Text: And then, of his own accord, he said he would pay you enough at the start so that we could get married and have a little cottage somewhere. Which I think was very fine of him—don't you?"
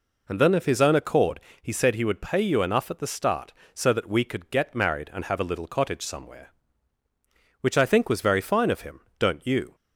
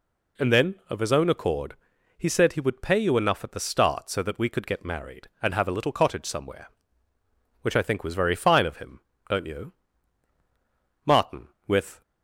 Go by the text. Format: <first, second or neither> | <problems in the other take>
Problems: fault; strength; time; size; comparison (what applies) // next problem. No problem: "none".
first | goes on to say "Martin with"; noticeable; from 11.0 s on; 0.96 s long